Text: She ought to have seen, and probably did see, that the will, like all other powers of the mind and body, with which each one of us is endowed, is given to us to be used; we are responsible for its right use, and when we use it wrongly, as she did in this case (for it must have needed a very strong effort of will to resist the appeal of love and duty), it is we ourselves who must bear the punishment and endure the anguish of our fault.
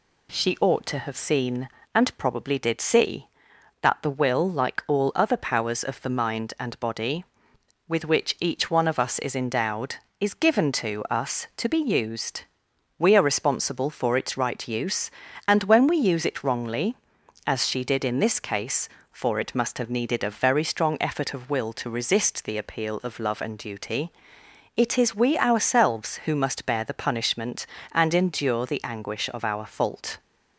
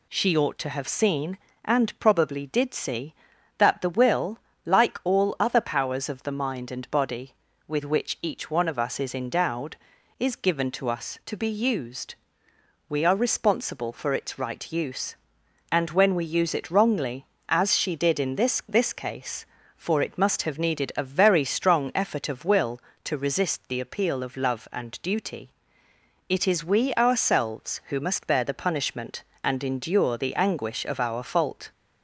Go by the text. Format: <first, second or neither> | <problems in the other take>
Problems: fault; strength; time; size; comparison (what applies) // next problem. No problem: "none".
first | says "this" twice; at 18.6 s